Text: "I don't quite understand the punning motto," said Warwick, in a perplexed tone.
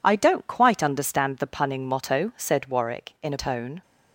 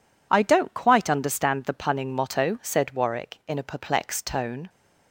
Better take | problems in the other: second | skips "perplexed"; at 3.3 s

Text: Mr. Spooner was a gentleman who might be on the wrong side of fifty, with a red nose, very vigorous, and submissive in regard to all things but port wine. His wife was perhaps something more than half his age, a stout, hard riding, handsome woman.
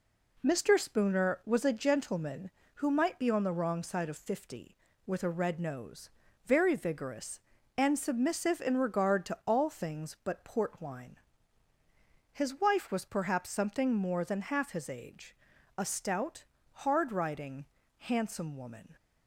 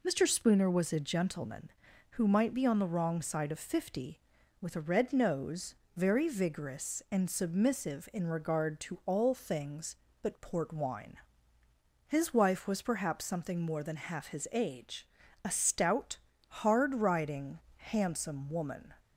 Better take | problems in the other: neither | none

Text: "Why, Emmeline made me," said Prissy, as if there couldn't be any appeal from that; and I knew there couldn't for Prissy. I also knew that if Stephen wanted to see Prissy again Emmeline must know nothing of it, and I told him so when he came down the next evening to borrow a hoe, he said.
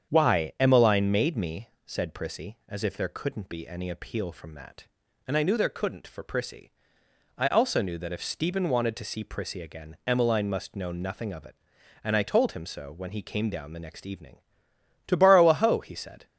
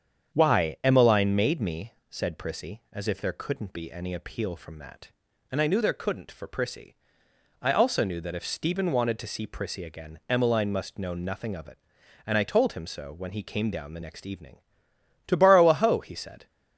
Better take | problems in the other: neither | starts louder than the rest; strong; the same in both

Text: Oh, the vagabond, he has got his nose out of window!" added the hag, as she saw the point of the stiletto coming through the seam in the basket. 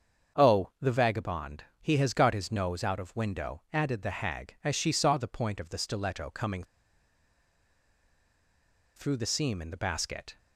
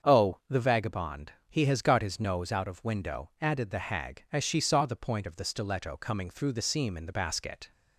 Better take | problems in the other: second | starts louder than the rest; until 1.4 s; 7 dB; also in the second // pauses between "coming" and "through"; strong; at 6.6 s; 2.3 s long

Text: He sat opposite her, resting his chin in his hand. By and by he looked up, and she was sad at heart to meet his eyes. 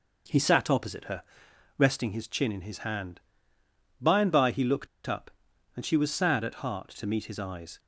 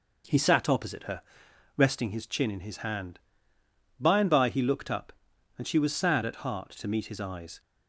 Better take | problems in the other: second | pauses between "looked" and "up"; slight; at 4.8 s; 0.18 s long

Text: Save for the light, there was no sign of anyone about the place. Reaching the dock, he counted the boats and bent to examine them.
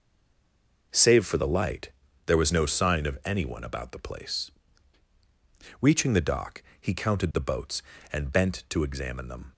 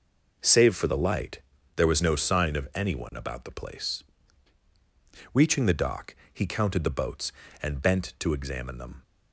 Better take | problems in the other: second | stays silent before the first word; slight; until 0.9 s; 0.9 s long

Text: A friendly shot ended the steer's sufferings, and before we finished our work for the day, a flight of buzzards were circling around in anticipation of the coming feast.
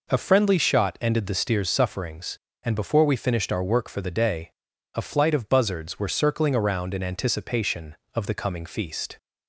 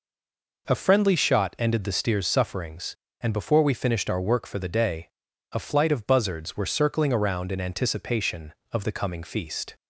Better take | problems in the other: first | stays silent before the first word; slight; until 0.6 s; 0.6 s long

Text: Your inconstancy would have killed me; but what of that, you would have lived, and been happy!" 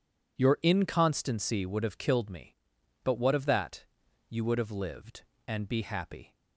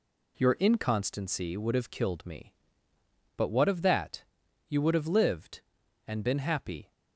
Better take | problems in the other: second | says "be" for "been"; at 5.6 s

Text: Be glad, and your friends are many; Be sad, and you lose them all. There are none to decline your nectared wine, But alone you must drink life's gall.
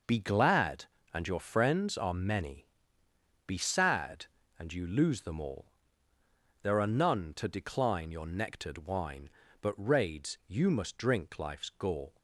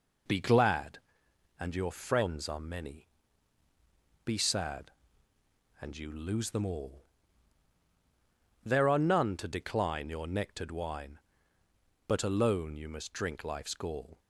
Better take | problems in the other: second | says "raids" for "alone"; at 9.7 s

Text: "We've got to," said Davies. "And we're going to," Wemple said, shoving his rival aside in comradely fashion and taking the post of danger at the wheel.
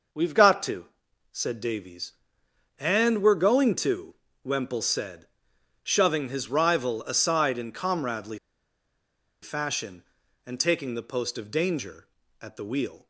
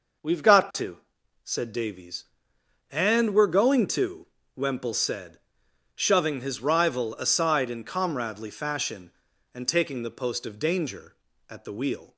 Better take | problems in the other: second | pauses between "comradely" and "fashion"; at 8.3 s; 1.0 s long

